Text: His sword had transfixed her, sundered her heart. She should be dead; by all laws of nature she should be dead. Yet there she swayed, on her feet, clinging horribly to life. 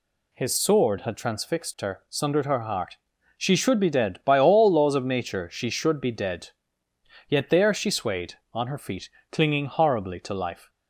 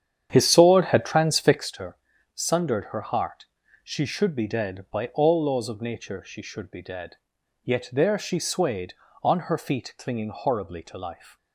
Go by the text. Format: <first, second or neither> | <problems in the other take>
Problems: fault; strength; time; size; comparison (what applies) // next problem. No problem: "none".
first | starts louder than the rest; strong; until 1.7 s; 9 dB